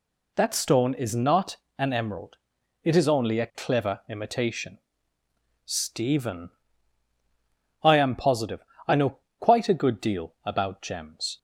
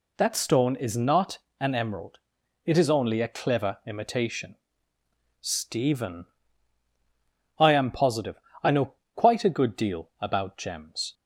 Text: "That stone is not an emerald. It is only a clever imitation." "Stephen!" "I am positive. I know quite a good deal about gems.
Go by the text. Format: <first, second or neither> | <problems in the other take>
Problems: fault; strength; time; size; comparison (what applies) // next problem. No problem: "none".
neither | pauses between "not" and "an"; slight; the same in both // pauses between "know" and "quite"; slight; the same in both